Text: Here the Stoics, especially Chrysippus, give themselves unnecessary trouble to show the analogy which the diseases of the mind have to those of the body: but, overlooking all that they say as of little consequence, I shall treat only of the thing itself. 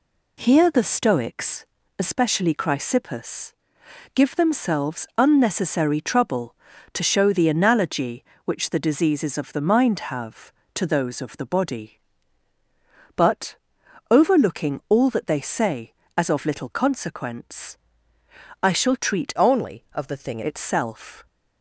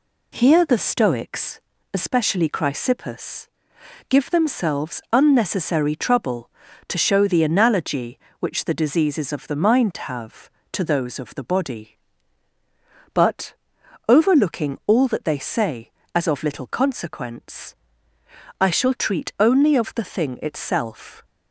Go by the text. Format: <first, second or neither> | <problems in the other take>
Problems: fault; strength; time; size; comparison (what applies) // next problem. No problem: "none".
second | changes voice from "only" to "thing"; from 19.3 to 20.4 s; 1.1 s long